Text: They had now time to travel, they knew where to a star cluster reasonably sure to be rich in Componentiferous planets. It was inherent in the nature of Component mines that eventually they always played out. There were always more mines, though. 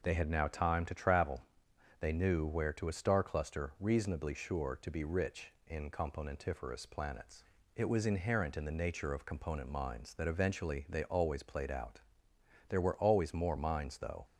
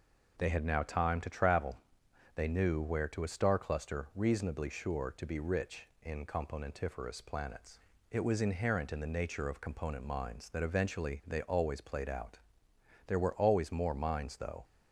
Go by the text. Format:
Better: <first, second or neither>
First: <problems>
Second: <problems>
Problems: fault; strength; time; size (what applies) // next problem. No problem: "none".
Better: neither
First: none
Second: none